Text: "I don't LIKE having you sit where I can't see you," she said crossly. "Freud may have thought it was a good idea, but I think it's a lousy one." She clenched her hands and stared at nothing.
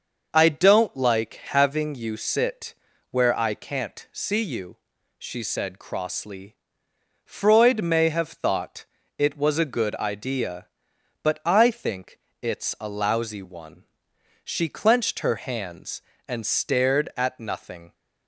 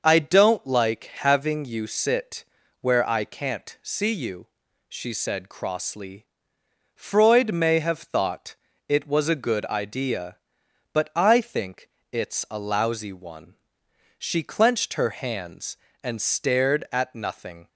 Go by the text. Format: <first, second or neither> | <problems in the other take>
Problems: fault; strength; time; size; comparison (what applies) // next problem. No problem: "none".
neither | starts louder than the rest; noticeable; the same in both // pauses between "sit" and "where"; slight; the same in both // pauses between "thought" and "it"; slight; the same in both // pauses between "think" and "it's"; slight; the same in both